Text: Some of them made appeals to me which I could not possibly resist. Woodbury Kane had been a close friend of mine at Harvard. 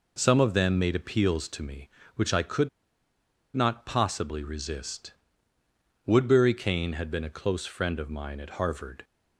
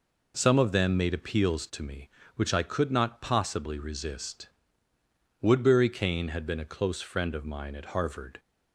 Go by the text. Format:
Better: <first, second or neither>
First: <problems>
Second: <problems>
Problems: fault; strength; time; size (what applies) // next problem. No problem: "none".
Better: second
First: pauses between "could" and "not"; noticeable; at 2.6 s; 0.86 s long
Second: none